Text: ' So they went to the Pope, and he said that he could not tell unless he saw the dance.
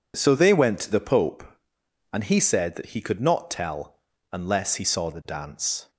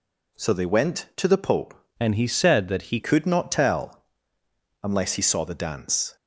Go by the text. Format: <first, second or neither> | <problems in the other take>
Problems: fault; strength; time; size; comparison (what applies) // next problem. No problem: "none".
first | changes voice from "and" to "he"; from 2.0 to 2.9 s; 0.9 s long // pauses between "tell" and "unless"; noticeable; at 4.0 s; 0.80 s long; slight in the first